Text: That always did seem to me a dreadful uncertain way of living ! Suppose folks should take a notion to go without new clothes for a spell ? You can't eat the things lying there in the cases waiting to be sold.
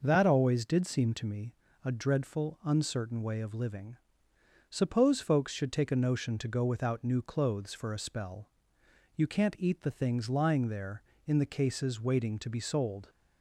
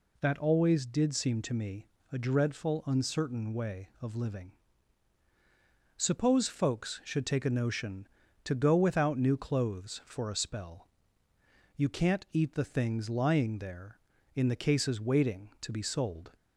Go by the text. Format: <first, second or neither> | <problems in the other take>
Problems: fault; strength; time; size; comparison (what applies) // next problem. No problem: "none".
neither | pauses between "me" and "a"; slight; the same in both